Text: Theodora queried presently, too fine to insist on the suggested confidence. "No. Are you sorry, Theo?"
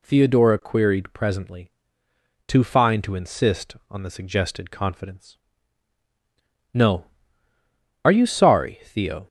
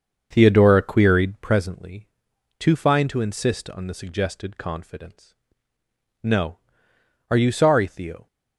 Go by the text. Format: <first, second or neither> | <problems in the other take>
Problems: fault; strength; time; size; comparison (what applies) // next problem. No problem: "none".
first | starts louder than the rest; until 1.5 s; 7 dB